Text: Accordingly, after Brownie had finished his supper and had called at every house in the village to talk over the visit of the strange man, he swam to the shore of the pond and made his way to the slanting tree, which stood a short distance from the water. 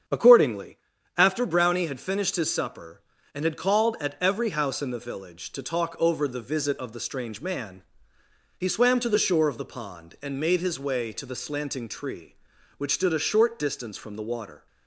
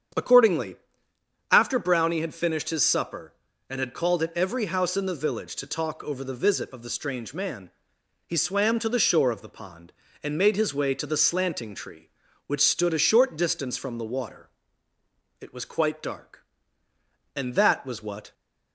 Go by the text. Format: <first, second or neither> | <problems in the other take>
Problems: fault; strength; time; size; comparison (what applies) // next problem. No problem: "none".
first | starts louder than the rest; strong; until 1.9 s; 8 dB; strong in the first // goes on to say "It was quite dark And that was what"; strong; from 15.4 s on; 2.9 s long